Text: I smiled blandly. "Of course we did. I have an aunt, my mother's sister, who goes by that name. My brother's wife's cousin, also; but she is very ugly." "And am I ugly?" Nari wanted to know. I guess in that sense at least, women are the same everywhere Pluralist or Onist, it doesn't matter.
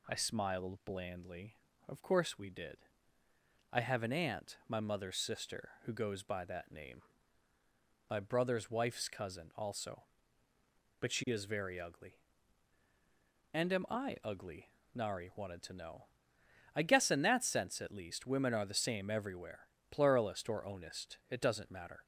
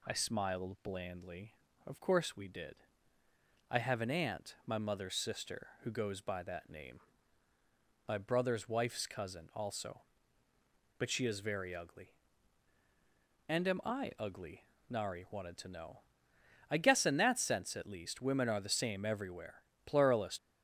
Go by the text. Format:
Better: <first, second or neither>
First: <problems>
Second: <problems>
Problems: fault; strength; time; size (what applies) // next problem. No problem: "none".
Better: first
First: pauses between "everywhere" and "Pluralist"; slight; at 19.6 s; 0.22 s long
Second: pauses between "everywhere" and "Pluralist"; slight; at 19.6 s; 0.22 s long // stops before "or Onist it doesn't matter"; at 20.3 s